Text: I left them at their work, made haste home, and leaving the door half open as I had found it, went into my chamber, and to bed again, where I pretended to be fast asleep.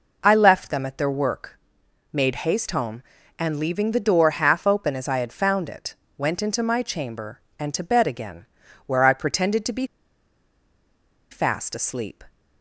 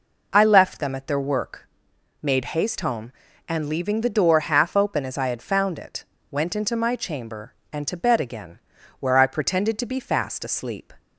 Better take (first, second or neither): second